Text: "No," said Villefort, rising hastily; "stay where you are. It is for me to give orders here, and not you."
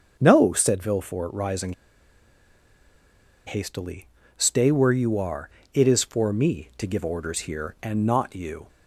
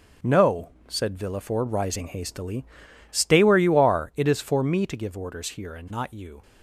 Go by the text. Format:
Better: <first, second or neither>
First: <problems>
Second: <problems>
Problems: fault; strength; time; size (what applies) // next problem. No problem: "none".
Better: second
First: starts louder than the rest; until 1.2 s; 6.5 dB // pauses between "rising" and "hastily"; strong; at 1.7 s; 1.7 s long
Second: starts louder than the rest; noticeable; until 1.4 s; 6 dB